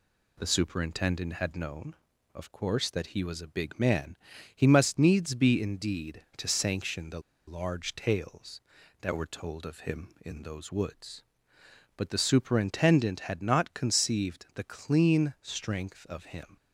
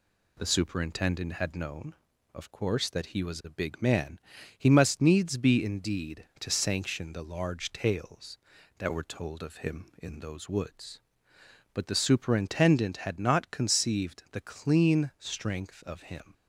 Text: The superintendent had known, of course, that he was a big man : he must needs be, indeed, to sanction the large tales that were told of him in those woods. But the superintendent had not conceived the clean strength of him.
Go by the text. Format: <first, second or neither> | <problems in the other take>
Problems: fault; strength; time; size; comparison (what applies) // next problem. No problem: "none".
second | pauses between "the" and "large"; slight; at 7.2 s; 0.26 s long